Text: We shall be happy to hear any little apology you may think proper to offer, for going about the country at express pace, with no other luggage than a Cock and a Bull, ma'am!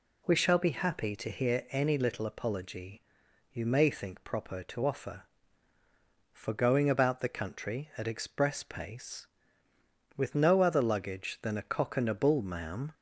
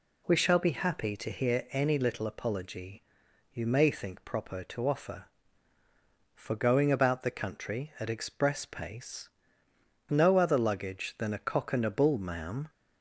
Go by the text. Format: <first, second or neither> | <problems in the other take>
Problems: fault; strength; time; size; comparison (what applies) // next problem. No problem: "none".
first | pauses between "apology" and "you"; noticeable; at 3.0 s; 0.50 s long; noticeable in the first // skips "with"; at 9.6 s